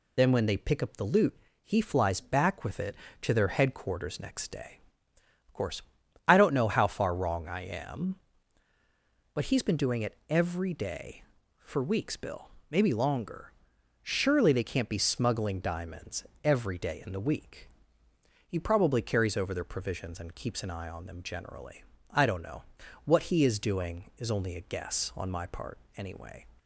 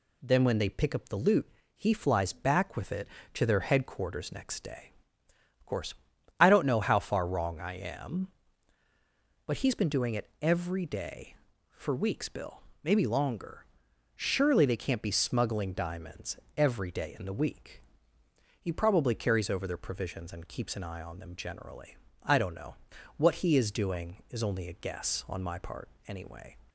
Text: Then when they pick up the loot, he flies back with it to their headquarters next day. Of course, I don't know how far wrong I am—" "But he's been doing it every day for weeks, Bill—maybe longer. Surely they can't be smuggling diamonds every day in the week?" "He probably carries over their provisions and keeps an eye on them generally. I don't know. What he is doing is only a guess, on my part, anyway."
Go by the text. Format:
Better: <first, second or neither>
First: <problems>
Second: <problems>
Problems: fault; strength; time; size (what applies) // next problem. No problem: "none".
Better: second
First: loses the start of "Then"; at 0.1 s; 80 ms // pauses between "diamonds" and "every"; slight; at 16.2 s; 0.20 s long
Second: pauses between "diamonds" and "every"; slight; at 16.3 s; 0.20 s long